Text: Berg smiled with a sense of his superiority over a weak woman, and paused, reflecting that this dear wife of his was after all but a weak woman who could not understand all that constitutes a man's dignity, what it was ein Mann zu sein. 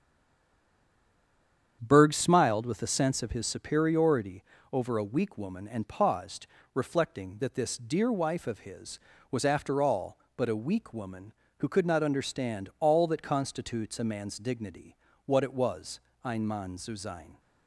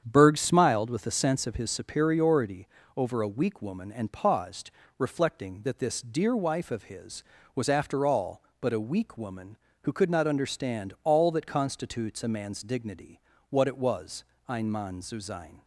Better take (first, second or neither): second